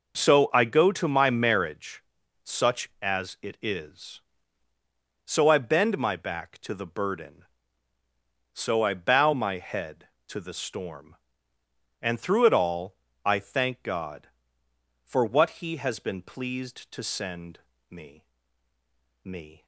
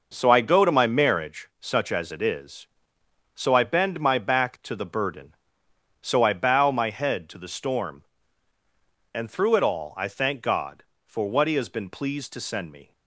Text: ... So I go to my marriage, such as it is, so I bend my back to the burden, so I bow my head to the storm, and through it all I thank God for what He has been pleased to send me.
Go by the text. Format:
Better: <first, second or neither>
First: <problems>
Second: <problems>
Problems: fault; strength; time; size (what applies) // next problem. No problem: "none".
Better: second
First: pauses between "all" and "I"; slight; at 12.9 s; 0.30 s long // pauses between "send" and "me"; slight; at 17.5 s; 0.30 s long // says "me" twice; at 19.2 s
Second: none